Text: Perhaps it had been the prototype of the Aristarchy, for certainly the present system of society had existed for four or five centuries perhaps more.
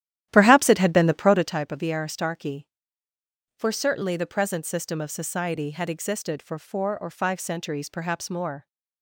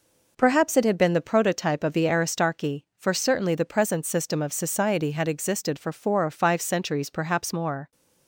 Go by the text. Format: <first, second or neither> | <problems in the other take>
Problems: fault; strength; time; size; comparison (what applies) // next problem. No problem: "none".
second | starts louder than the rest; strong; until 1.6 s; 12.5 dB